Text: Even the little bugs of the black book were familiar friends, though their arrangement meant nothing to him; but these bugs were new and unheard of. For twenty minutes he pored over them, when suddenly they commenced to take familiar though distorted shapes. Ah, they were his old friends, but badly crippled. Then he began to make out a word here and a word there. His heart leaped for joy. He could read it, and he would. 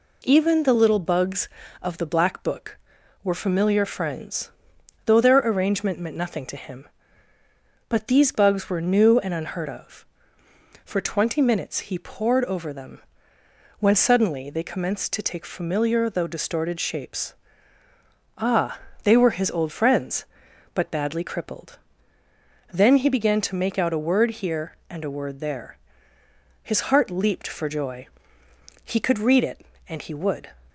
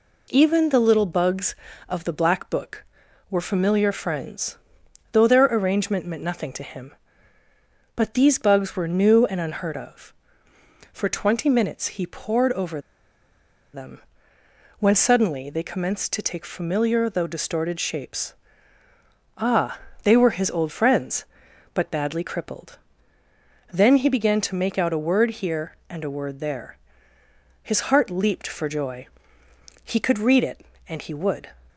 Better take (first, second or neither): first